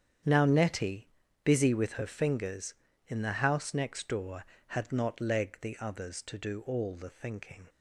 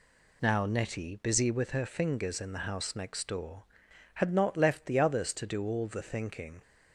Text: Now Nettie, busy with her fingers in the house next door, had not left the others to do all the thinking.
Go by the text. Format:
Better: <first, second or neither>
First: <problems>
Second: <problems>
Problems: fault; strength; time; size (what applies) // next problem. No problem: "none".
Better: second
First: starts louder than the rest; strong; until 1.5 s; 8.5 dB // says "leg" for "left"; at 5.1 s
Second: none